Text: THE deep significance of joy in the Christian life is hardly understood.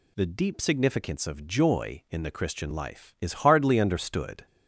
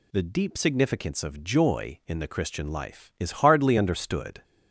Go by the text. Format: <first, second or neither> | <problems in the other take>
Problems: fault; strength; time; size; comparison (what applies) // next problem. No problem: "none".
neither | none